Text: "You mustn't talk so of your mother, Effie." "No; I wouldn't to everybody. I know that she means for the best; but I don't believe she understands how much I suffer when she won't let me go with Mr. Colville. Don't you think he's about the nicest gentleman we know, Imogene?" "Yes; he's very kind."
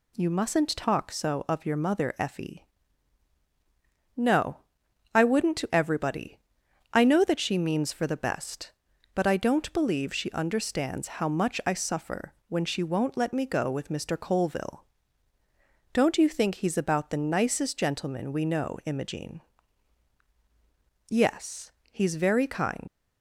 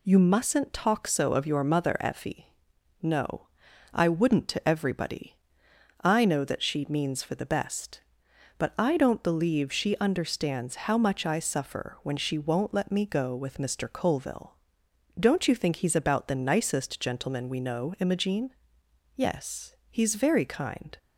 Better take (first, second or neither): second